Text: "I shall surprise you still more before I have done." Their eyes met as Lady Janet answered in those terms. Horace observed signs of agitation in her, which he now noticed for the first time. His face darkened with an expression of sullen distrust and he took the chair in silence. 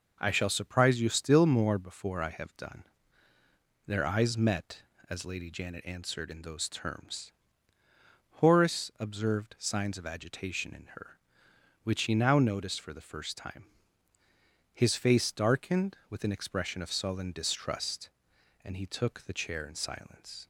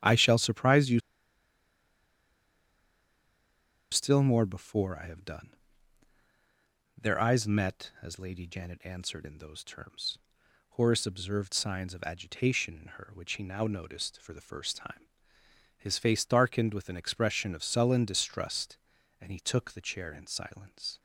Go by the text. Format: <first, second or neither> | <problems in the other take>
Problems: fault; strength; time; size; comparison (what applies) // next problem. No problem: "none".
first | starts louder than the rest; strong; until 3.9 s; 11 dB // pauses between "you" and "still"; strong; at 0.9 s; 2.9 s long